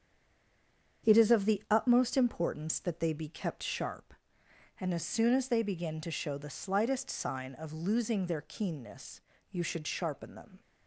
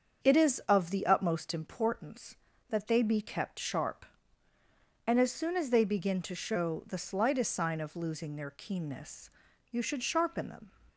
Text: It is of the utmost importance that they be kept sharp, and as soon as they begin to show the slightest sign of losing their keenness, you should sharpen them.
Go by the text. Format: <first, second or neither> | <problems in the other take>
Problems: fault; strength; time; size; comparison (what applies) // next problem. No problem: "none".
second | stays silent before the first word; until 1.0 s; 1.0 s long // starts louder than the rest; strong; until 2.1 s; 7.5 dB; strong in the second